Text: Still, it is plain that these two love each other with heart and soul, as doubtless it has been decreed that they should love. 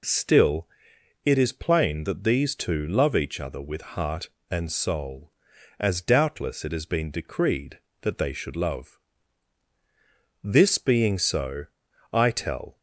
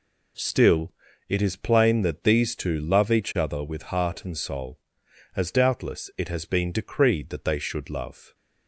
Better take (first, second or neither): second